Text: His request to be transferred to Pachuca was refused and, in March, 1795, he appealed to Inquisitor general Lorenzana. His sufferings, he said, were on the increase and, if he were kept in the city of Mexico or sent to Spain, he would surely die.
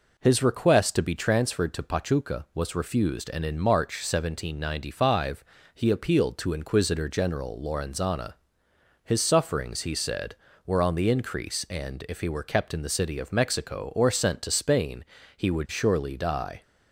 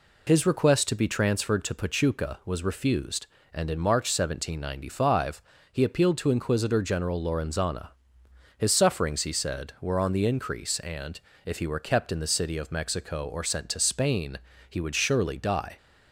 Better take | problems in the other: neither | none

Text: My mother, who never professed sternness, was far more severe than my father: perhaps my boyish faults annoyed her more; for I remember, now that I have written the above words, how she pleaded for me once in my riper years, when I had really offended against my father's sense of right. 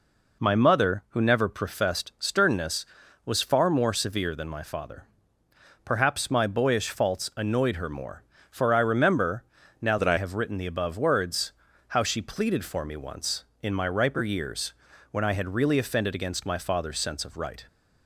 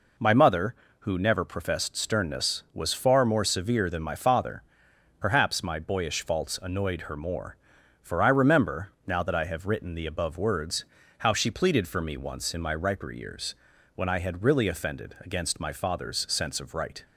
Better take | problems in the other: second | changes voice from "that" to "I"; from 9.9 to 10.1 s; 0.2 s long

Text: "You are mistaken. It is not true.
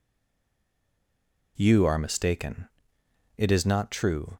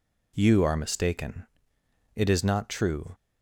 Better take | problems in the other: second | stays silent before the first word; noticeable; until 1.5 s; 1.5 s long

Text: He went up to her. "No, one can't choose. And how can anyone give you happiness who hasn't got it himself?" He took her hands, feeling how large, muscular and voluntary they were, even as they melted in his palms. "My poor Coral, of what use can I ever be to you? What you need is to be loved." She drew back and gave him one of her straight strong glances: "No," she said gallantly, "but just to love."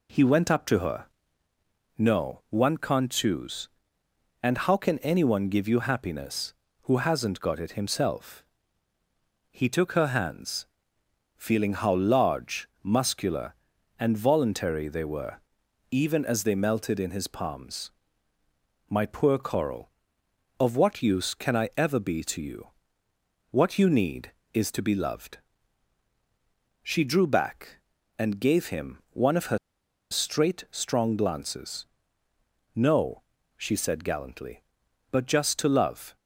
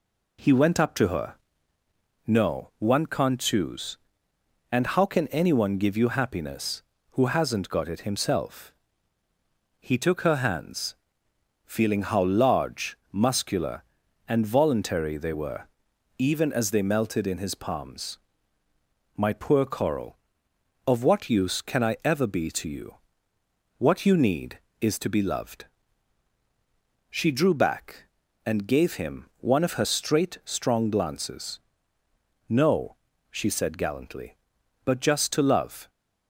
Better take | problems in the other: second | pauses between "her" and "straight"; noticeable; at 29.5 s; 0.54 s long

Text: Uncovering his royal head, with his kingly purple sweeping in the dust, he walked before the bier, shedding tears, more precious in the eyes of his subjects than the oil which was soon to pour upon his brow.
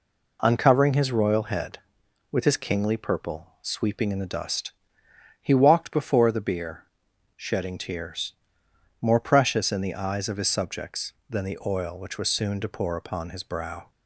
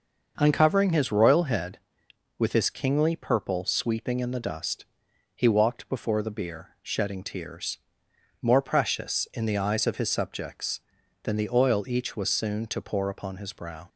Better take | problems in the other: first | starts louder than the rest; noticeable; until 1.3 s; 6 dB // says "each" for "which"; at 11.8 s

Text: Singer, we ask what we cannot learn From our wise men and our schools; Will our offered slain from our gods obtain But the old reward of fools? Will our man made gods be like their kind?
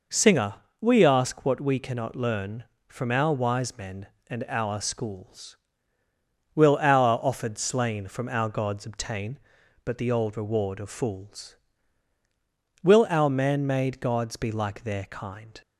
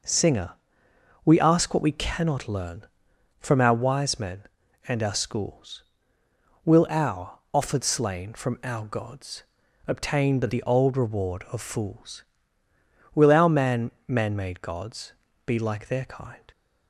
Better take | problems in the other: first | pauses between "gods" and "obtain"; at 9.4 s; 0.42 s long // says "man" twice; at 14.0 s // pauses between "gods" and "be"; slight; at 15.1 s; 0.34 s long

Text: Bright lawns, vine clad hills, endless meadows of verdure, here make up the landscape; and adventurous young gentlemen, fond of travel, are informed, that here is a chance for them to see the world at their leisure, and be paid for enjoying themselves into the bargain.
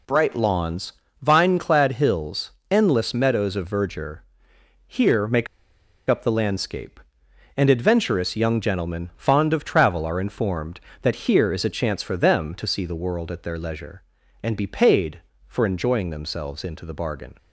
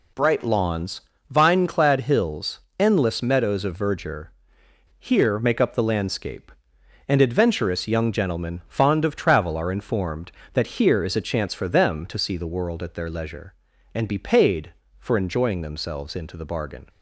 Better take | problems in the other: second | pauses between "make" and "up"; noticeable; at 5.4 s; 0.62 s long

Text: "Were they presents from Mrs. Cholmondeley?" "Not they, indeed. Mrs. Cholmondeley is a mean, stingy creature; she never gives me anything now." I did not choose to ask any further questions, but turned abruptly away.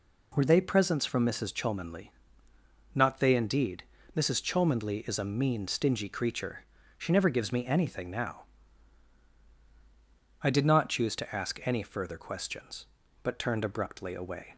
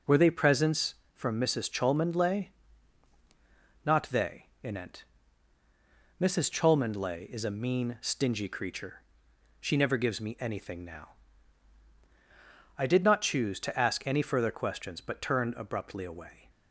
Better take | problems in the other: first | says "inent" for "indeed"; at 4.6 s

